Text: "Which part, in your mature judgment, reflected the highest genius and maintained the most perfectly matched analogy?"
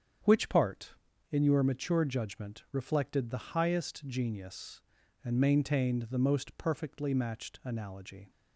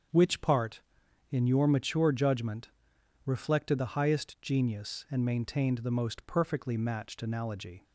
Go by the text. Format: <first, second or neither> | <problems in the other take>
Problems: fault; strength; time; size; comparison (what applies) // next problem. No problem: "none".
neither | starts louder than the rest; strong; the same in both